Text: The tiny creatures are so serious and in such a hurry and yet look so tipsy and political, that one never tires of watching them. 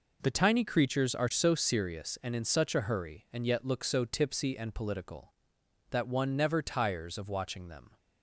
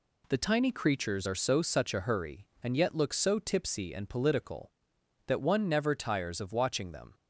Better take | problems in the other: first | skips "serious and in"; at 1.6 s

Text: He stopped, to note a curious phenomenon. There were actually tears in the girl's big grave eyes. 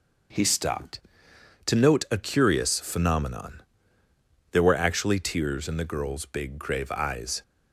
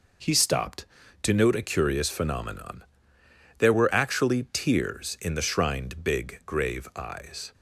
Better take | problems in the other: first | says "shrined" for "girl's"; at 5.4 s

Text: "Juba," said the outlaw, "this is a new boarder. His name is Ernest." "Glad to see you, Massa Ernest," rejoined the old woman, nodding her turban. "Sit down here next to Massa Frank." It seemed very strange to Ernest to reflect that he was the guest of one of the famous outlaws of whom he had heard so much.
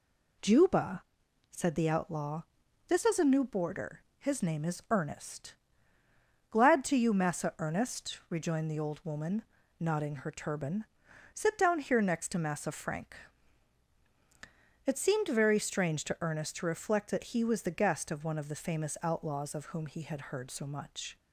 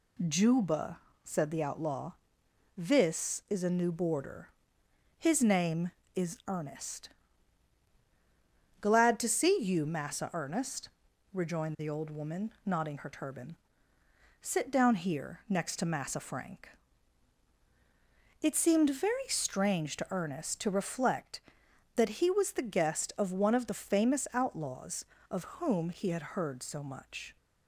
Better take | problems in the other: second | skips "see"; at 6.9 s

